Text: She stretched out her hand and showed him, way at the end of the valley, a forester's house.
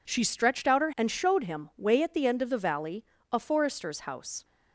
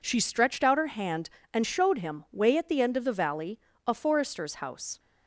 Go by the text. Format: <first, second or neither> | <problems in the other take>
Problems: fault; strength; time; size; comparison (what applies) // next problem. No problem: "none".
second | skips "hand"; at 0.9 s